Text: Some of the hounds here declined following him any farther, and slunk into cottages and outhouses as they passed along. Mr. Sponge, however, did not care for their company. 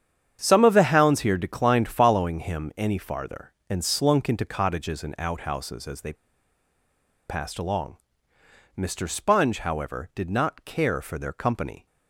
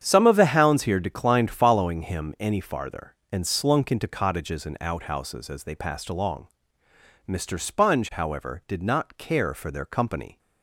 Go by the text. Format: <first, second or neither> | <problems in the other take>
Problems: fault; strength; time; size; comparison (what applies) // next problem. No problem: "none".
second | starts louder than the rest; strong; until 1.4 s; 8.5 dB; strong in the second // pauses between "they" and "passed"; at 6.1 s; 1.1 s long